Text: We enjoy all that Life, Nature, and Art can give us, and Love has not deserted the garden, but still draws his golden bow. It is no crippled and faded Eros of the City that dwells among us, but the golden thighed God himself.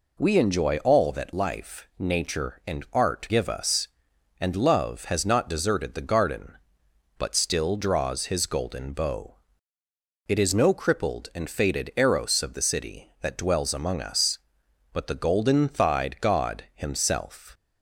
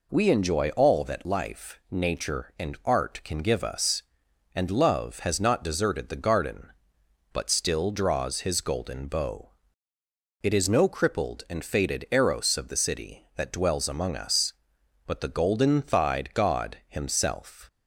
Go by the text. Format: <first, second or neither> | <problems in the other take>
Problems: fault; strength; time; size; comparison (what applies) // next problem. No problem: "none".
second | skips "can"; at 3.2 s